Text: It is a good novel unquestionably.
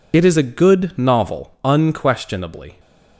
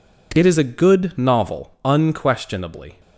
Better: second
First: loses the start of "It"; at 0.1 s; 50 ms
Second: none

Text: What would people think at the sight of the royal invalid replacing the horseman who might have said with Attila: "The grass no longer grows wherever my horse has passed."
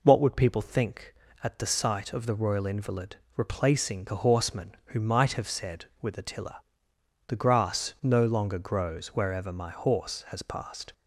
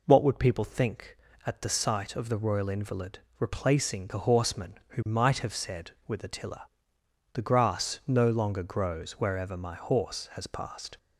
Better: neither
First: pauses between "invalid" and "replacing"; slight; at 3.1 s; 0.20 s long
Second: pauses between "invalid" and "replacing"; slight; at 3.1 s; 0.20 s long

